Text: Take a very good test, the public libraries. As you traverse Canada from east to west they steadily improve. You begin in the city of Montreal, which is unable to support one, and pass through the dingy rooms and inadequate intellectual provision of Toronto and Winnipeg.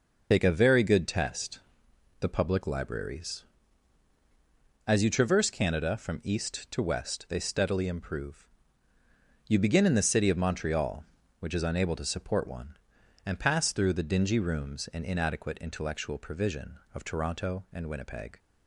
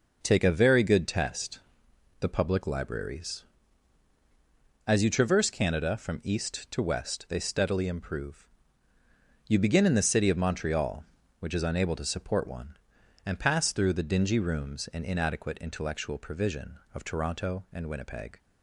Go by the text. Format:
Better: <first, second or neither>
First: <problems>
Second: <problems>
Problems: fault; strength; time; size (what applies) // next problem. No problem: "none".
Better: second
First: loses the start of "Take"; at 0.3 s; 85 ms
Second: none